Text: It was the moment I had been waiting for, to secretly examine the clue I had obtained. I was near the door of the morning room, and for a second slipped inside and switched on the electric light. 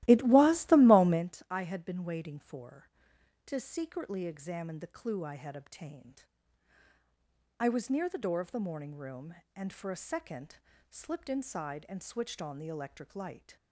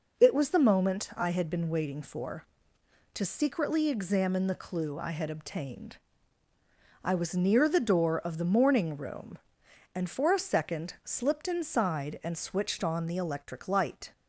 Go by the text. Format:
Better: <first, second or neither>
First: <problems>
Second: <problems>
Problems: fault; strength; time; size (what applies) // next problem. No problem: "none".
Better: second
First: starts louder than the rest; strong; until 1.4 s; 15.5 dB // pauses between "second" and "slipped"; slight; at 10.5 s; 0.34 s long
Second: none